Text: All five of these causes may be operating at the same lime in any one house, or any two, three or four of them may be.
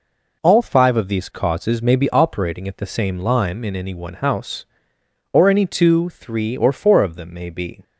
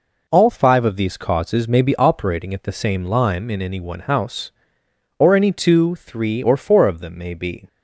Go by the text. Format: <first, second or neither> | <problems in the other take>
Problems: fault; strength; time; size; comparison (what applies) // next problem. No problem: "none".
neither | none